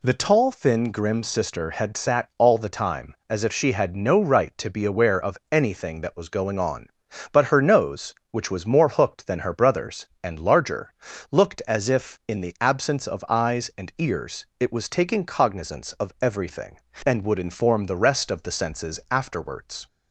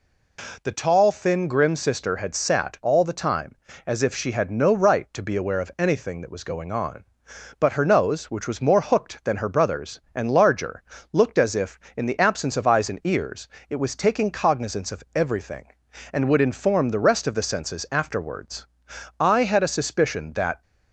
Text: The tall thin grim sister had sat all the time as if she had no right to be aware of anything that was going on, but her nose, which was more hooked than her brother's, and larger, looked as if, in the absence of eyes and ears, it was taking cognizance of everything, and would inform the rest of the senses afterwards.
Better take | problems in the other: first | goes on to say "I had a suspicion that"; from 19.1 s on; 1.4 s long

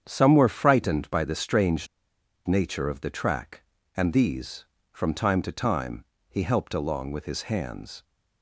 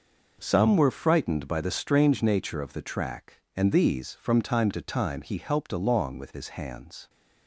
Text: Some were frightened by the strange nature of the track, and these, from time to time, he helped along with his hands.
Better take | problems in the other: second | starts louder than the rest; strong; until 1.0 s; 8 dB // pauses between "strange" and "nature"; noticeable; at 1.8 s; 0.60 s long

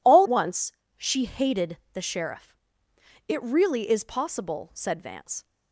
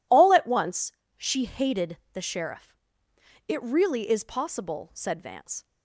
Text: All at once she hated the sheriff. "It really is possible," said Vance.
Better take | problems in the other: second | skips "at"; at 0.2 s // pauses between "once" and "she"; slight; at 0.7 s; 0.24 s long; slight in the second // pauses between "hated" and "the"; slight; at 1.7 s; 0.16 s long; slight in the second

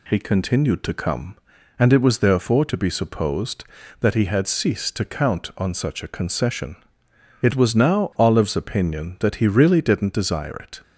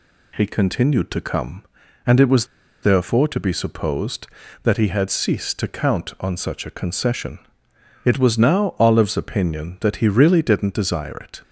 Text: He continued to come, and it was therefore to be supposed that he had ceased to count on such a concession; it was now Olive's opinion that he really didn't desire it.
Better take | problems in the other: first | pauses between "was" and "therefore"; at 2.4 s; 0.36 s long

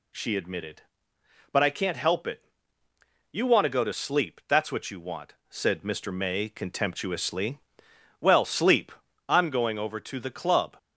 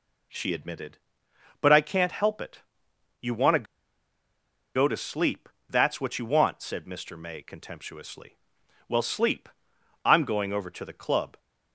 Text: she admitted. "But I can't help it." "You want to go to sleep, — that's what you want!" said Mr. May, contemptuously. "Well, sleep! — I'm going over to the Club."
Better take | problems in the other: first | pauses between "to" and "go"; at 3.6 s; 1.1 s long

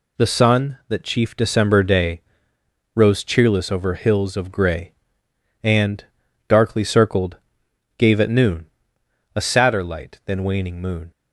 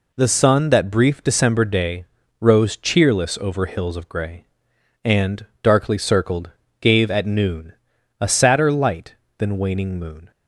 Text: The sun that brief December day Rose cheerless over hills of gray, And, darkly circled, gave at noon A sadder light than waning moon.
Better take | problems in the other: second | says "chief" for "brief"; at 1.0 s // pauses between "day" and "Rose"; noticeable; at 2.2 s; 0.74 s long; slight in the second // pauses between "noon" and "A"; noticeable; at 8.6 s; 0.68 s long; also in the second

